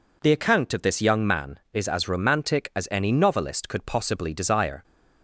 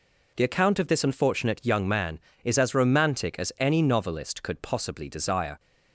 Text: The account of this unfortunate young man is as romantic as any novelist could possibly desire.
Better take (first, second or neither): second